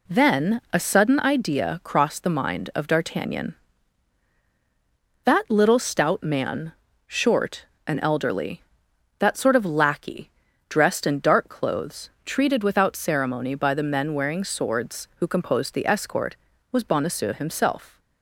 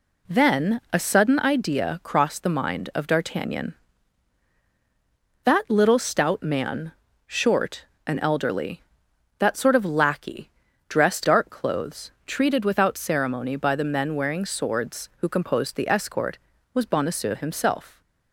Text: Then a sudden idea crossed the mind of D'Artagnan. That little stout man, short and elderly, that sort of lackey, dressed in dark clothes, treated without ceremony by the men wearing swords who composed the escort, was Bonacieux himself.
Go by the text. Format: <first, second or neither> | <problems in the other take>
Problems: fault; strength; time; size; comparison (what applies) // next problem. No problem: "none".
first | skips "in"; at 11.2 s